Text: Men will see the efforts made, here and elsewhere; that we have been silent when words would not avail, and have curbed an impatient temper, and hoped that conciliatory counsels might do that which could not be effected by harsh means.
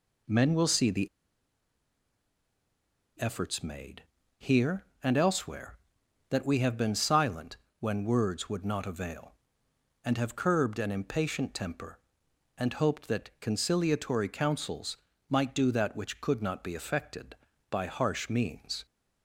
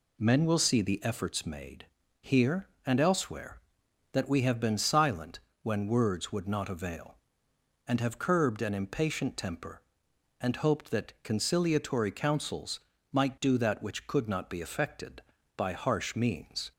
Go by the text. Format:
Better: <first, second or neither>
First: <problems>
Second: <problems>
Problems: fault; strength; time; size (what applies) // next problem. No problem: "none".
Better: second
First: pauses between "the" and "efforts"; strong; at 1.0 s; 2.1 s long // pauses between "silent" and "when"; slight; at 7.5 s; 0.24 s long // pauses between "counsels" and "might"; slight; at 14.9 s; 0.32 s long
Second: pauses between "silent" and "when"; slight; at 5.4 s; 0.24 s long // pauses between "counsels" and "might"; slight; at 12.7 s; 0.32 s long